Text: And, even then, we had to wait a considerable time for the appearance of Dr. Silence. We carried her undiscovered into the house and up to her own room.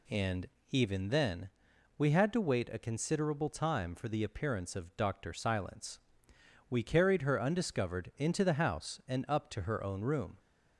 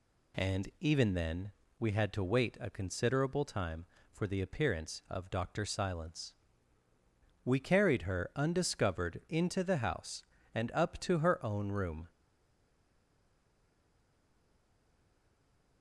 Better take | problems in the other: first | stays silent after the last word; strong; from 12.0 s on; 3.8 s long

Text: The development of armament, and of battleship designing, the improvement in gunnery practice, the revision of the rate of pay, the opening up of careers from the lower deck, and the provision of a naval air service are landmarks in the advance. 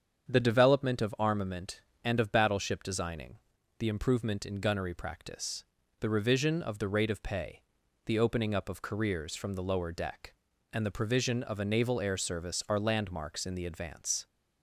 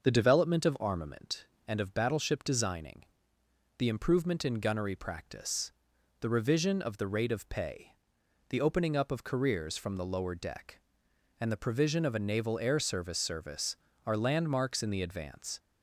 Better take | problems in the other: first | starts louder than the rest; until 1.0 s; 6 dB; strong in the first // says "service" twice; at 13.1 s

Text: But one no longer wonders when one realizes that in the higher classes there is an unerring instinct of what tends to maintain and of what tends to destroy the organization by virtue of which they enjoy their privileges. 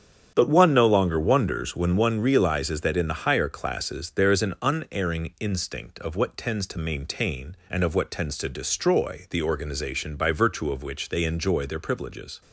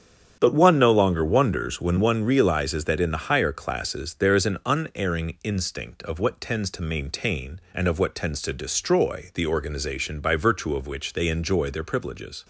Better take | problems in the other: neither | starts louder than the rest; strong; the same in both

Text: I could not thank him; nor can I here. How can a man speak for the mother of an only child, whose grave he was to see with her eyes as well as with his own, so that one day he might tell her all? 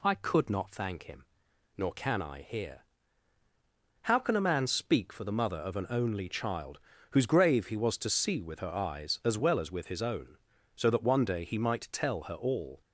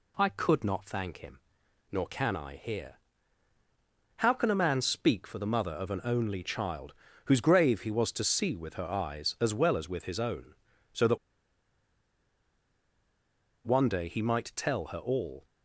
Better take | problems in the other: first | pauses between "that" and "one"; strong; at 11.1 s; 2.4 s long

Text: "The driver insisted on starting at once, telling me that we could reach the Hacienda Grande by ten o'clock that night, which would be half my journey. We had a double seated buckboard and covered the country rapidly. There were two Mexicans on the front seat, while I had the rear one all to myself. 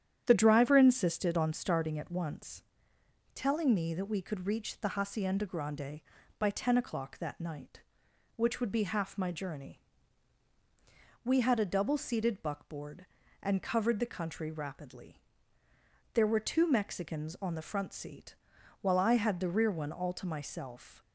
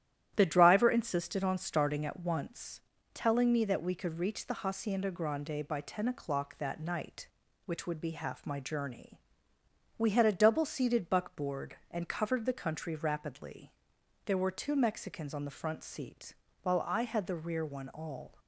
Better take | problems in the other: first | starts louder than the rest; strong; until 1.3 s; 12 dB; strong in the first // stops before "to myself"; at 18.3 s

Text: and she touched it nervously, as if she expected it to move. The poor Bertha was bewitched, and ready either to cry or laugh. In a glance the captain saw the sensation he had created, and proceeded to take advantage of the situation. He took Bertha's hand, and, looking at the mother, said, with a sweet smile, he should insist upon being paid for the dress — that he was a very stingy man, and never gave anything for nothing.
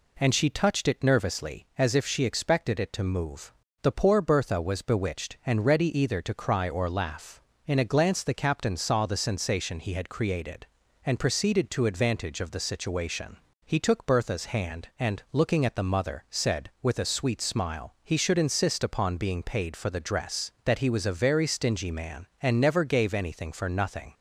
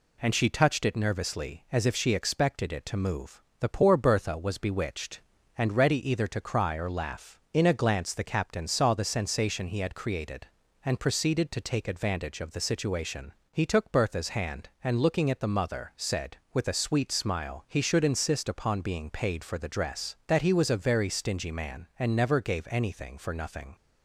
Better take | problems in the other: second | skips "take"; at 11.8 s

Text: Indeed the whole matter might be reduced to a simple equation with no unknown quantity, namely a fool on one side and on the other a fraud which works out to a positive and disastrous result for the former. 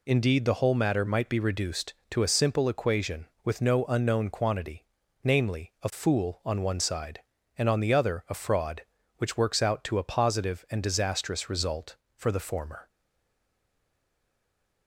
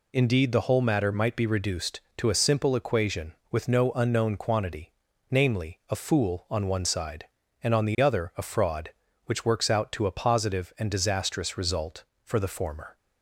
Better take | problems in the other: second | stays silent after the last word; noticeable; from 12.8 s on; 2.0 s long

